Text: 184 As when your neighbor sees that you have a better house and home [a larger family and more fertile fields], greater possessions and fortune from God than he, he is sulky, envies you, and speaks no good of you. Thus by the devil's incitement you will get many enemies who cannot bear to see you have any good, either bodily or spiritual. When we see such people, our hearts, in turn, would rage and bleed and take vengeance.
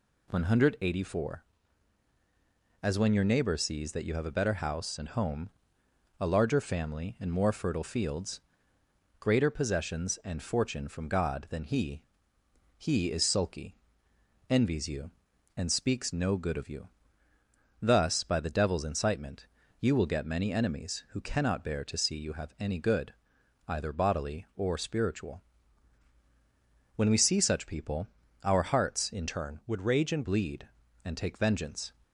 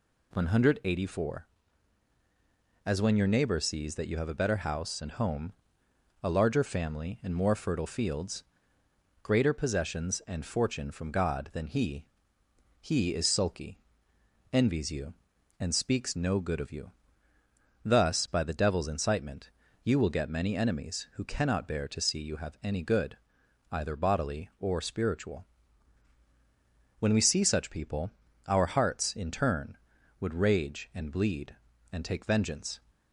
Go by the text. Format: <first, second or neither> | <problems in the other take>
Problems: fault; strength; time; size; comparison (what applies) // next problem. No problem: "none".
second | pauses between "home" and "a"; noticeable; at 5.4 s; 0.72 s long; noticeable in the second // pauses between "incitement" and "you"; slight; at 19.4 s; 0.34 s long; slight in the second // changes voice from "turn" to "and"; from 29.2 to 30.2 s; 1.0 s long